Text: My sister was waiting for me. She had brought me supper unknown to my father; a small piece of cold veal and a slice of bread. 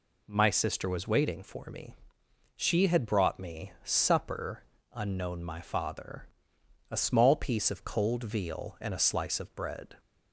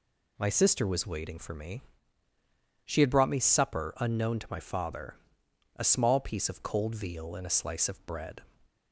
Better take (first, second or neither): second